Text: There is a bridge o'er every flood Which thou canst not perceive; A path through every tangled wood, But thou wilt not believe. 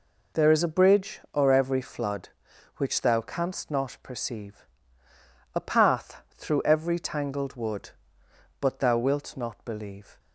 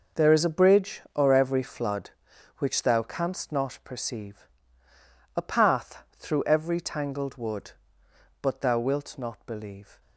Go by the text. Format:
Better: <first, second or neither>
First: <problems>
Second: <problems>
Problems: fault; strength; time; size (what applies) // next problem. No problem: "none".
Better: first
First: pauses between "path" and "through"; slight; at 6.2 s; 0.16 s long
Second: gets quieter; strong; throughout; 12 dB // pauses between "path" and "through"; slight; at 6.0 s; 0.16 s long